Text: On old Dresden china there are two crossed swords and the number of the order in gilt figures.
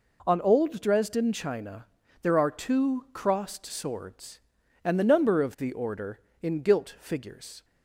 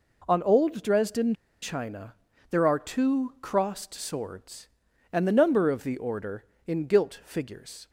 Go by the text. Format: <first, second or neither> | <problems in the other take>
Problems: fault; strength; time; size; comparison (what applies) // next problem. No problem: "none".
first | pauses between "Dresden" and "china"; slight; at 1.3 s; 0.27 s long // pauses between "china" and "there"; slight; at 2.1 s; 0.34 s long; slight in the first